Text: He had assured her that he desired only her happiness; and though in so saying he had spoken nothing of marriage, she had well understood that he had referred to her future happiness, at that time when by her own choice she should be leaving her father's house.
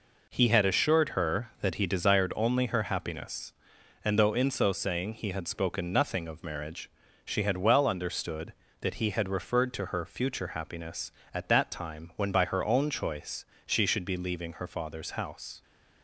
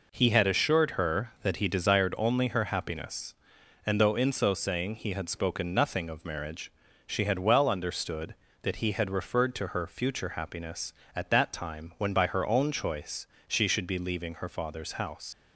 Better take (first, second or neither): first